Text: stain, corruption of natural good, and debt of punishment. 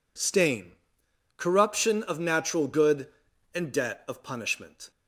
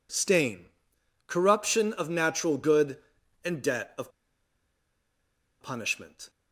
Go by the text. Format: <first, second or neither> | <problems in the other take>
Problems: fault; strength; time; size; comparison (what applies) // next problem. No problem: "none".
first | pauses between "of" and "punishment"; strong; at 4.1 s; 1.5 s long